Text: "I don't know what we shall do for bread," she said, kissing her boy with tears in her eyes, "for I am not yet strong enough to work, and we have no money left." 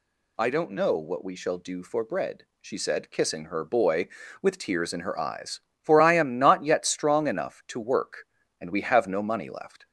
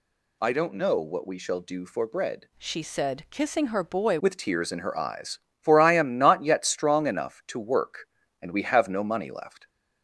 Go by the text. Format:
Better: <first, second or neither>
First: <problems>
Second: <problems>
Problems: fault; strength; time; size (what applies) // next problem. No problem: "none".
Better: first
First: none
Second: changes voice from "she" to "boy"; from 2.5 to 4.1 s; 1.6 s long